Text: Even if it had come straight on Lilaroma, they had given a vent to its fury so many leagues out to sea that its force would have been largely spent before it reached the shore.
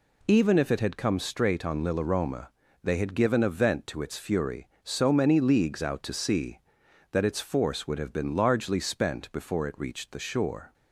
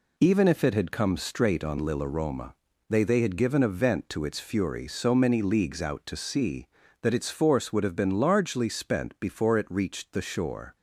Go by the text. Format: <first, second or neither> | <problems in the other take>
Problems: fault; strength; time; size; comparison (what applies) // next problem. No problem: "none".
first | says "they" twice; at 3.0 s